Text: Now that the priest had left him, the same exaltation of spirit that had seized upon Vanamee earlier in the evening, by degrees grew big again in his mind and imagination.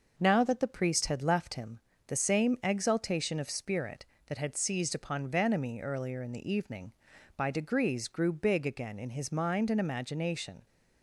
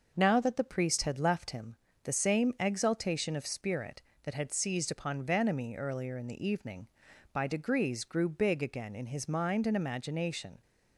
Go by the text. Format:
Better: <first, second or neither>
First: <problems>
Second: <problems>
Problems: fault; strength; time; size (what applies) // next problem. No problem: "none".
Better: neither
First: starts louder than the rest; noticeable; until 1.2 s; 6 dB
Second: starts louder than the rest; noticeable; until 1.1 s; 6 dB